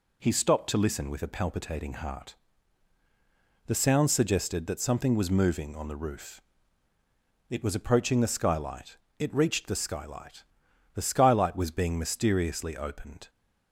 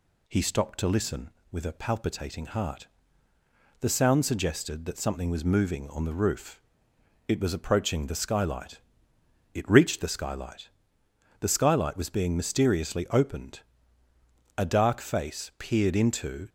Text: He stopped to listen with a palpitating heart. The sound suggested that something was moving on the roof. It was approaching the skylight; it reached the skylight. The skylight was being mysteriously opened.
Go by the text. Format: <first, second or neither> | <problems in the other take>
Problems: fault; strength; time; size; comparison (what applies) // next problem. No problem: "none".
first | goes on to say "A dark face peered into"; strong; from 14.5 s on; 1.9 s long